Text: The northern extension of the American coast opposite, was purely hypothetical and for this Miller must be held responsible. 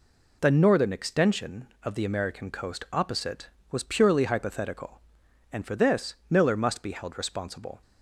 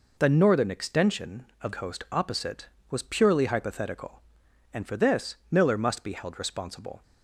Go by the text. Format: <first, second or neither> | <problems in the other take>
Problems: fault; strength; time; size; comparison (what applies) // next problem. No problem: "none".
first | skips "the American"; at 1.7 s